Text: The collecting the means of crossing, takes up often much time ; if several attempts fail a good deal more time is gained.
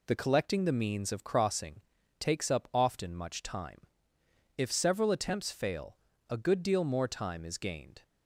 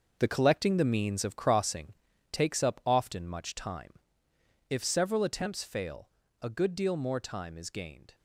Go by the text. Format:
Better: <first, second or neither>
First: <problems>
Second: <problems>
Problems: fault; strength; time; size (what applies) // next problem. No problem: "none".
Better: first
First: pauses between "fail" and "a"; slight; at 5.9 s; 0.32 s long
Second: gets quieter; strong; throughout; 9.5 dB // pauses between "fail" and "a"; slight; at 6.0 s; 0.32 s long